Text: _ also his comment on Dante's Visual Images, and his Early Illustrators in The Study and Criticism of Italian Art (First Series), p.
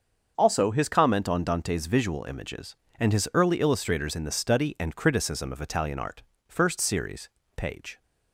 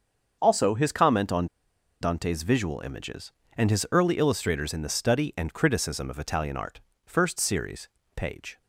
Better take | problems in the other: first | starts louder than the rest; until 1.4 s; 6.5 dB; also in the first // pauses between "on" and "Dante's"; noticeable; at 1.4 s; 0.54 s long

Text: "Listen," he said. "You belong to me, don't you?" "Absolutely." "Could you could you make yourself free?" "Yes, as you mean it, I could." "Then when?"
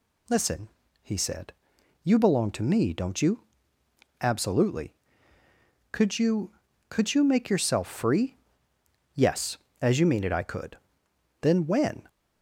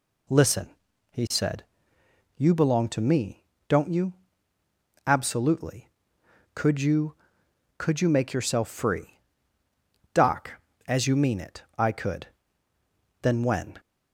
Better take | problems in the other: first | says "Doc" for "Yes"; at 10.1 s

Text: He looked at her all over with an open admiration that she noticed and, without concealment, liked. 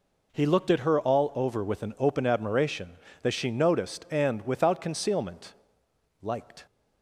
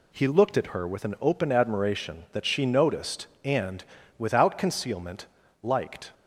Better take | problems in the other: first | skips "all over"; at 0.8 s

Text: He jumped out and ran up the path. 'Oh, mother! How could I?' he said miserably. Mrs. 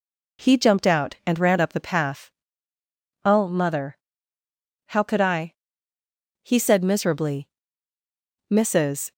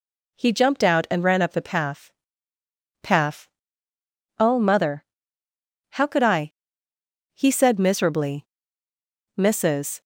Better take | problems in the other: first | says "path" twice; at 3.0 s

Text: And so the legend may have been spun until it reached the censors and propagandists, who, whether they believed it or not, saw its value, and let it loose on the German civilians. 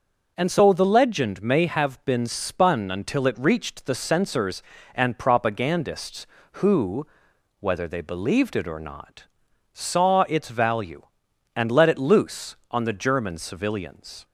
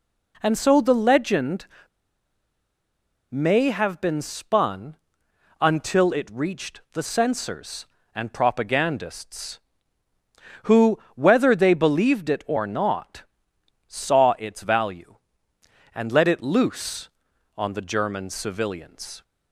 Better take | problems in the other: first | pauses between "legend" and "may"; strong; at 1.6 s; 1.6 s long // pauses between "spun" and "until"; noticeable; at 4.9 s; 0.64 s long

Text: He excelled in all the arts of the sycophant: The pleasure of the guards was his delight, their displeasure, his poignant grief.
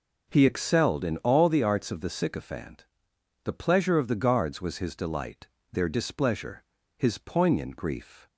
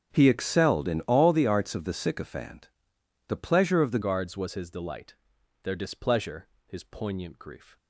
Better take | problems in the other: first | starts louder than the rest; until 1.1 s; 7 dB // changes voice at "guards"; from 4.0 s on; 3.7 s long

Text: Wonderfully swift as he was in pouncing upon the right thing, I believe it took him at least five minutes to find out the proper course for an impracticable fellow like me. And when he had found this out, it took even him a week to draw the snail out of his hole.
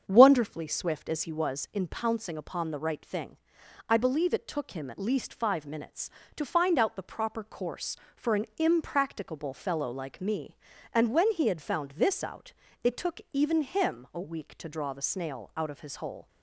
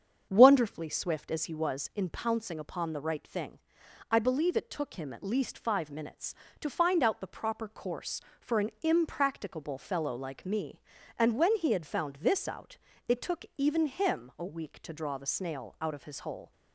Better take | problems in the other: neither | starts louder than the rest; strong; the same in both

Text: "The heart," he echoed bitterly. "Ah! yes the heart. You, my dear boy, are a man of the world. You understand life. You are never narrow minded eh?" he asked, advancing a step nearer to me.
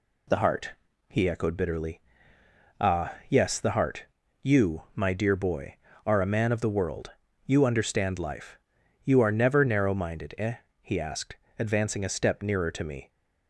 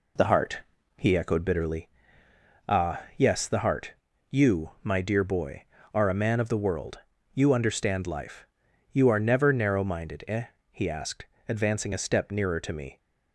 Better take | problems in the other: first | starts louder than the rest; slight; until 1.9 s; 3 dB

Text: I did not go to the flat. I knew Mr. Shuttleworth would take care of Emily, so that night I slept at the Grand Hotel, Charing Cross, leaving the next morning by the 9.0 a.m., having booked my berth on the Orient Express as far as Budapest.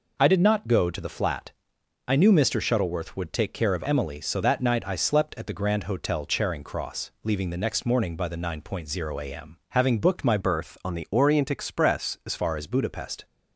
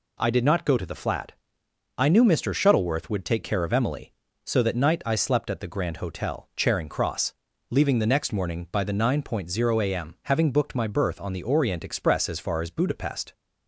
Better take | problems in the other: second | changes voice from "berth" to "as"; from 10.4 to 12.3 s; 1.9 s long

